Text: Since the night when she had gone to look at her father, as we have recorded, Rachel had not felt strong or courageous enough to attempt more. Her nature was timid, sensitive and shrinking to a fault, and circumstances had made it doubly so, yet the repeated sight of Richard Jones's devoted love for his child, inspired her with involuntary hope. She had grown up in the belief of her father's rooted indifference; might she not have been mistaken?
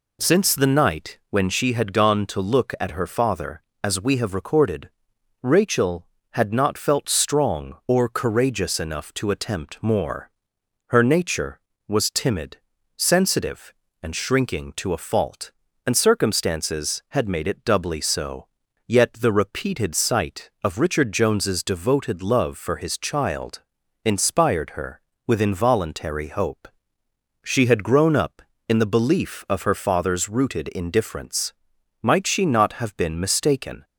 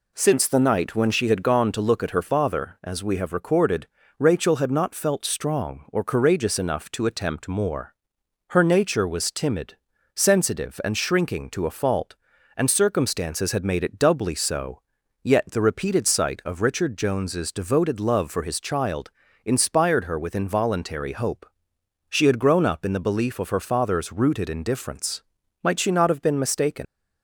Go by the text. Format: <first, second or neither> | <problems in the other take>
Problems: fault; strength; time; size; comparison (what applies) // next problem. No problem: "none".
first | leaves "mistaken" unfinished; at 26.8 s; 140 ms